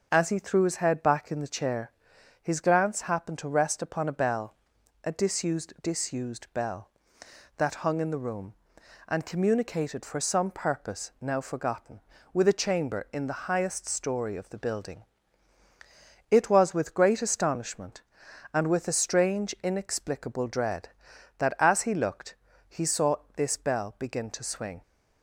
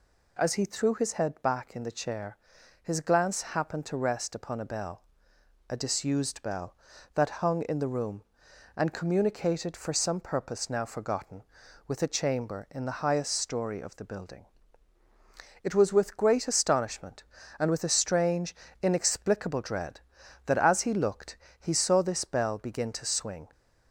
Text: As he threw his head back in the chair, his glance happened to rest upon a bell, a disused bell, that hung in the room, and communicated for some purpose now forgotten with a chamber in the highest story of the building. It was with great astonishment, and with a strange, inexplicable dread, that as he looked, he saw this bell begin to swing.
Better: second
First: says "disused" twice; at 5.8 s // pauses between "saw" and "this"; slight; at 23.1 s; 0.18 s long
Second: none

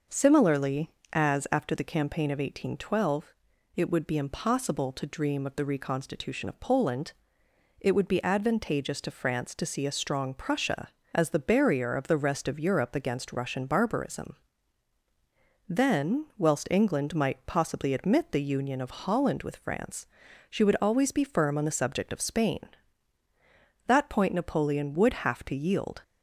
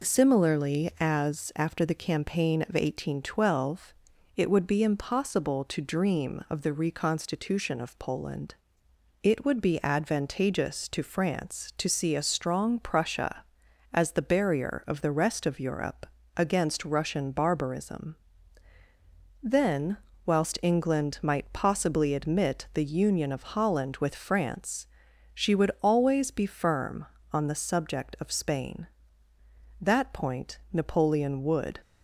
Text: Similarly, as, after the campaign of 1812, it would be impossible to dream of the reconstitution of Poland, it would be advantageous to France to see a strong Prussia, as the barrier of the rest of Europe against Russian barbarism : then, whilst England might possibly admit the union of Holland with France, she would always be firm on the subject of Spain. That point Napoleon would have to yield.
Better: first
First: none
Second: pauses between "Europe" and "against"; slight; at 16.0 s; 0.28 s long // pauses between "point" and "Napoleon"; slight; at 30.5 s; 0.16 s long // stops before "have to yield"; at 31.8 s

